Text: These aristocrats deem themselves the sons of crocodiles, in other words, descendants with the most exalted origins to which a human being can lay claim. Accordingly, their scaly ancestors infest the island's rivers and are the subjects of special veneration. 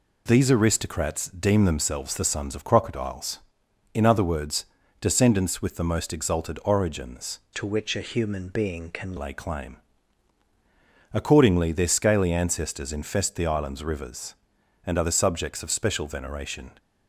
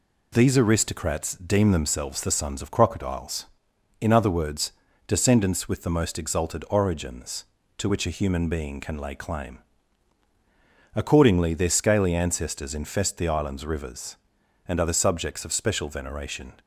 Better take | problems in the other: second | changes voice from "to" to "can"; from 7.5 to 9.1 s; 1.6 s long

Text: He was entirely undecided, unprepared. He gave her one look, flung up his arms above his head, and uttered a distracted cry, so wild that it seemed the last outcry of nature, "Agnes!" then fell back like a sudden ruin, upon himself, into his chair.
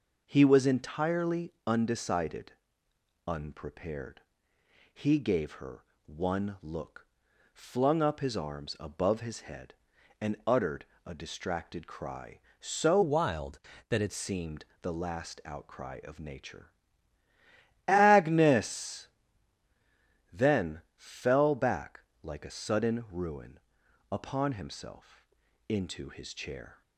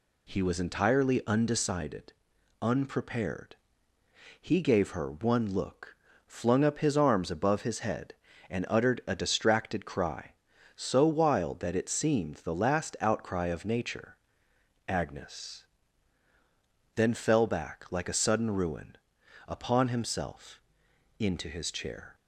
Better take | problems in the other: second | pauses between "her" and "one"; slight; at 5.8 s; 0.22 s long // pauses between "uttered" and "a"; slight; at 10.8 s; 0.20 s long // changes voice from "wild" to "it"; from 13.0 to 14.1 s; 1.1 s long // pauses between "seemed" and "the"; slight; at 14.6 s; 0.18 s long // pauses between "back" and "like"; slight; at 21.9 s; 0.24 s long

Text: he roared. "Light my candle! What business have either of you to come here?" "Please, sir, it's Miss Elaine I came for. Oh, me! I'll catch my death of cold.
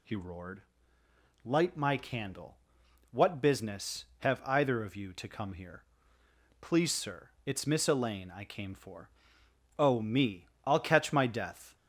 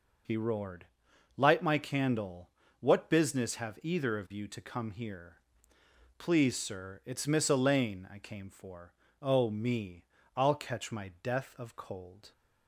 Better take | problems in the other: second | stops before "of cold"; at 11.7 s

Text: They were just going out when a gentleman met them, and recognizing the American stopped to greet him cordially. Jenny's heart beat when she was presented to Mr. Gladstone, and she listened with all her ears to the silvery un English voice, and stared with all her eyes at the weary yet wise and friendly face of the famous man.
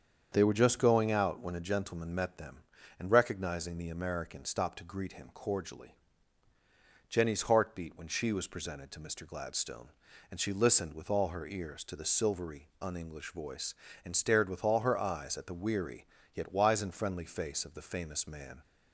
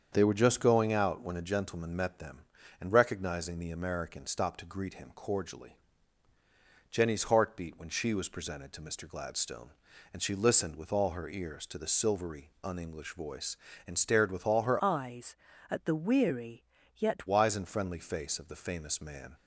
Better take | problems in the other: first | starts louder than the rest; strong; until 1.1 s; 7.5 dB; strong in the first // changes voice from "eyes" to "yet"; from 14.8 to 17.2 s; 2.4 s long // pauses between "weary" and "yet"; slight; at 16.6 s; 0.32 s long; slight in the first

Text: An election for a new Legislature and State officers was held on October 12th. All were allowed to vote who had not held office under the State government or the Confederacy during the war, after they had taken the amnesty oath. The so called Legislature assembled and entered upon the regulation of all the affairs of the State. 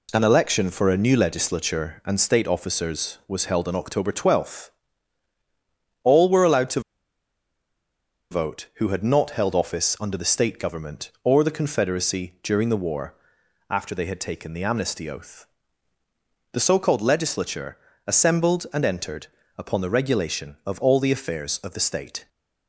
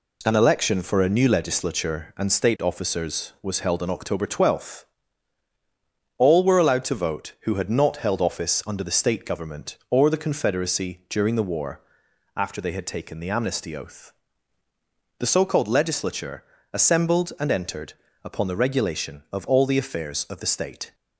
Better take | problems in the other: second | pauses between "to" and "vote"; strong; at 6.7 s; 1.5 s long // pauses between "Legislature" and "assembled"; slight; at 17.7 s; 0.30 s long; slight in the second // pauses between "entered" and "upon"; slight; at 19.2 s; 0.30 s long; slight in the second

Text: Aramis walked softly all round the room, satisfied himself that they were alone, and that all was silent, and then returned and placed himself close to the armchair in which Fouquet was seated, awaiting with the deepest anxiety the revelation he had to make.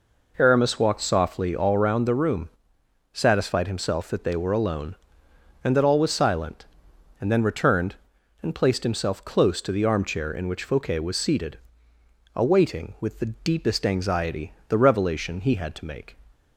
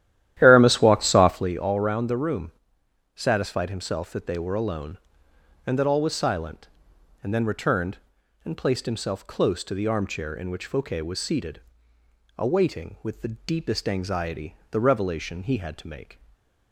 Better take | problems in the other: first | starts louder than the rest; strong; until 1.6 s; 12.5 dB // pauses between "anxiety" and "the"; slight; at 14.5 s; 0.16 s long; slight in the first // stays silent after the last word; slight; from 16.1 s on; 0.6 s long

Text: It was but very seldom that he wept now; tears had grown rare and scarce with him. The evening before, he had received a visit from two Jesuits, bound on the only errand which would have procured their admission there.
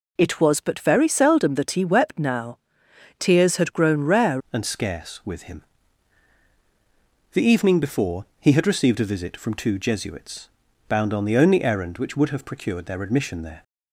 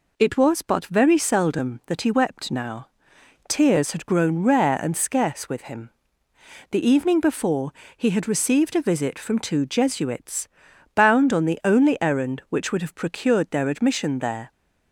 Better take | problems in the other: second | changes voice at "and"; from 4.5 s on; 9.1 s long

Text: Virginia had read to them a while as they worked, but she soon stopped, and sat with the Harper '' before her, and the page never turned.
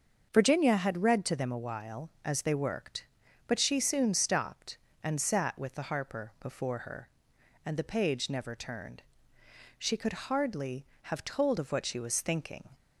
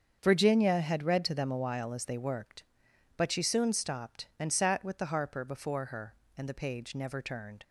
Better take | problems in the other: second | starts louder than the rest; until 1.3 s; 6.5 dB; also in the second // goes on to say "She could hardly have told of what she was thinking"; strong; from 9.7 s on; 2.9 s long

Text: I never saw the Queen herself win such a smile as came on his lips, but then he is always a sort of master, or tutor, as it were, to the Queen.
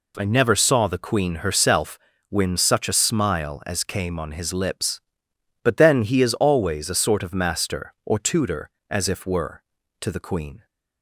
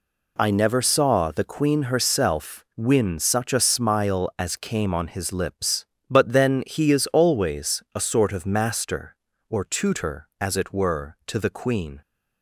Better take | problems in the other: second | pauses between "herself" and "win"; slight; at 1.9 s; 0.32 s long // says "if" for "it"; at 9.0 s

